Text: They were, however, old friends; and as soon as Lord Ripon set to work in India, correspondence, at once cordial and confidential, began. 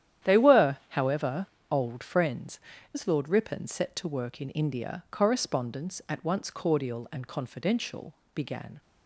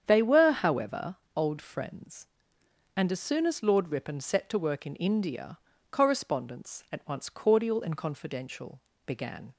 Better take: second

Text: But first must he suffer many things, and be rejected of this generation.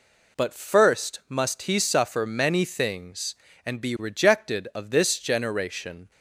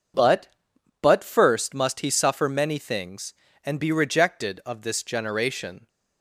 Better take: first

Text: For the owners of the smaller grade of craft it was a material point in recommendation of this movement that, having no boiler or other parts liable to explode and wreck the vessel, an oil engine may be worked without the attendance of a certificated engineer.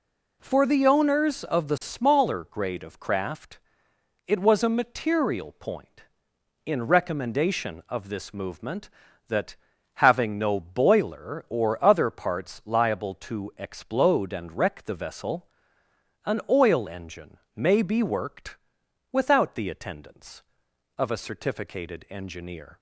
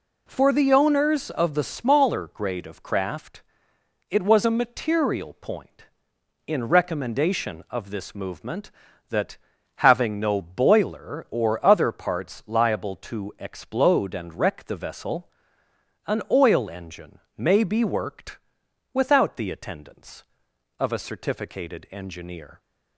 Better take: neither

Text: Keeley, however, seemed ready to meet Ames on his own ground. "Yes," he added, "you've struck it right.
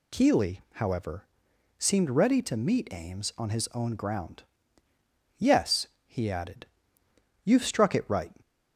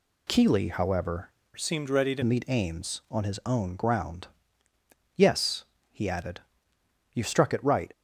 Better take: first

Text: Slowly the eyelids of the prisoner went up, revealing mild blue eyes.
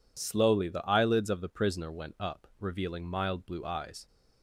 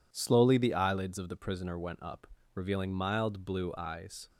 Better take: neither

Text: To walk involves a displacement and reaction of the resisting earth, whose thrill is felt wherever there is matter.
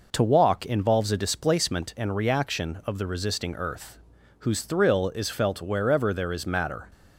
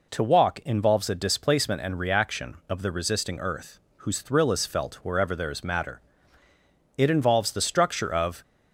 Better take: first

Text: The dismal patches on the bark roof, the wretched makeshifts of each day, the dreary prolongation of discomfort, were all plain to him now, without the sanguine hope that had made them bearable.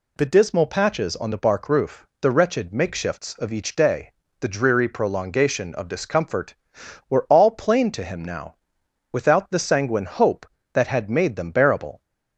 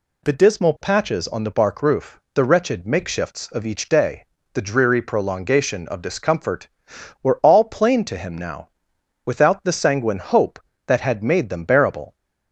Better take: neither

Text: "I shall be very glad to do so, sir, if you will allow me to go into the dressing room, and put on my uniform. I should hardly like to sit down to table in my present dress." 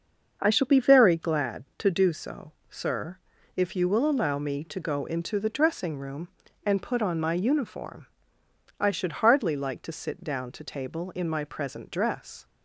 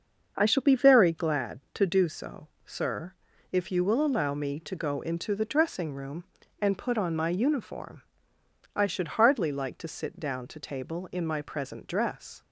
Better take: neither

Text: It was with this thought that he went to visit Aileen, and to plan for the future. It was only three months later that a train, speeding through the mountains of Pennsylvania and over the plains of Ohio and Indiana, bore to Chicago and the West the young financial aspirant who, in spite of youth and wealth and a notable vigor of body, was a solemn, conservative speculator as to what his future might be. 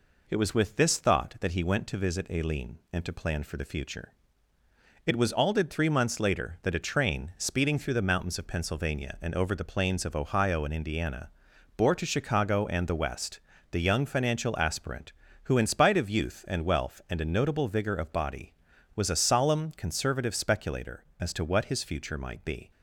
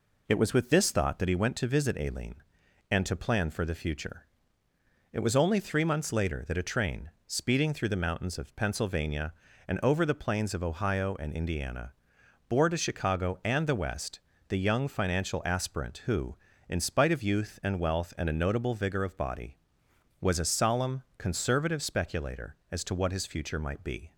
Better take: second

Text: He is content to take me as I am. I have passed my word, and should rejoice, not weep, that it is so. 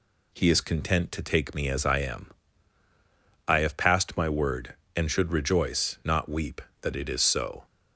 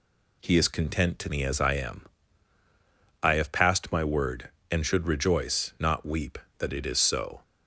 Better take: first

